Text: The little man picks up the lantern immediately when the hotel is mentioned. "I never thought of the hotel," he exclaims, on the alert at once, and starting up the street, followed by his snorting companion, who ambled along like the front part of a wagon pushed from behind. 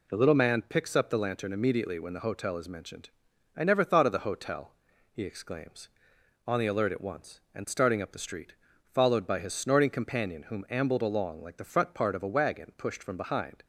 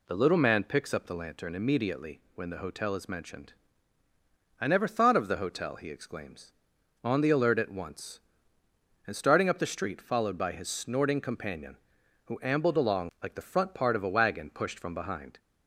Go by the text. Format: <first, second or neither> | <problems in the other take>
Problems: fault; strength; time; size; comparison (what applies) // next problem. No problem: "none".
second | says "whom" for "who"; at 10.4 s